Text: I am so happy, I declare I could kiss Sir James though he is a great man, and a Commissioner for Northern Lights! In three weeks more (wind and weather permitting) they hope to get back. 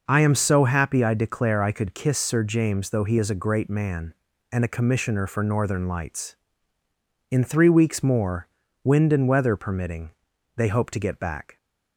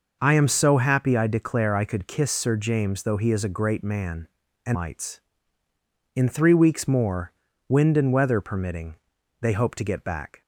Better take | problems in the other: first | skips "a Commissioner for Northern"; at 4.7 s

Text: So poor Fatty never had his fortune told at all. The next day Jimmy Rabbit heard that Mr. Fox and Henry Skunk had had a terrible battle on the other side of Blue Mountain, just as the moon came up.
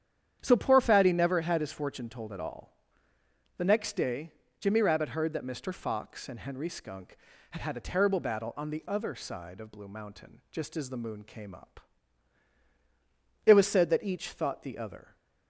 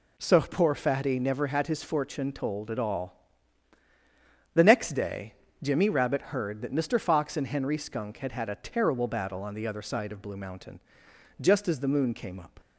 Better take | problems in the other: second | starts louder than the rest; strong; until 1.4 s; 9.5 dB // pauses between "day" and "Jimmy"; slight; at 4.3 s; 0.28 s long; slight in the second // goes on to say "It was said that each thought the other"; strong; from 13.4 s on; 1.7 s long

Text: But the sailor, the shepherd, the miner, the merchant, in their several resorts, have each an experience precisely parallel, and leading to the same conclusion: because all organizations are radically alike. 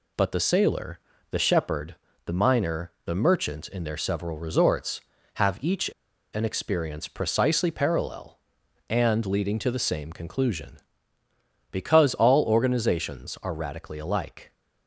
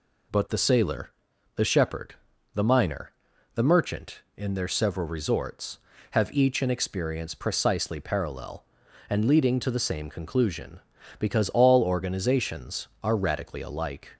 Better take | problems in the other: second | pauses between "each" and "an"; at 5.9 s; 0.44 s long

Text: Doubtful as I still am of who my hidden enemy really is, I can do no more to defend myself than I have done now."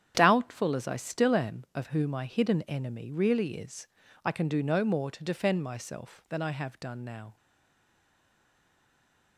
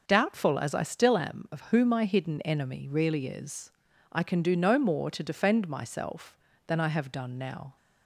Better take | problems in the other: second | starts louder than the rest; strong; until 1.1 s; 9.5 dB; noticeable in the second // stays silent after the last word; noticeable; from 7.3 s on; 2.0 s long

